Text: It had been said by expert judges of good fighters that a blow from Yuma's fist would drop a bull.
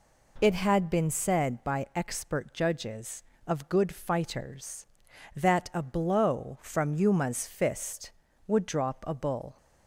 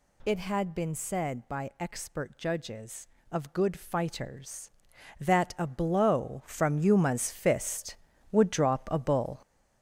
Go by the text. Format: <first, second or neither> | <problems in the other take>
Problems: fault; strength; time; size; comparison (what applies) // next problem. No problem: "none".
first | gets louder; throughout; 7 dB